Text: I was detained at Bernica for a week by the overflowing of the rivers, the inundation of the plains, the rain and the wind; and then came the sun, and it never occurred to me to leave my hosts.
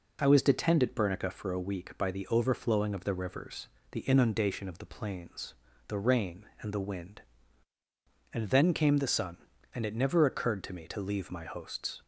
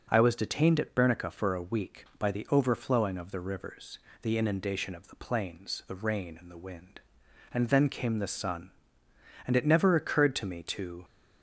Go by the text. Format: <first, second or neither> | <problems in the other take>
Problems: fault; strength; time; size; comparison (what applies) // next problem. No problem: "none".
first | stops before "leave my hosts"; at 11.0 s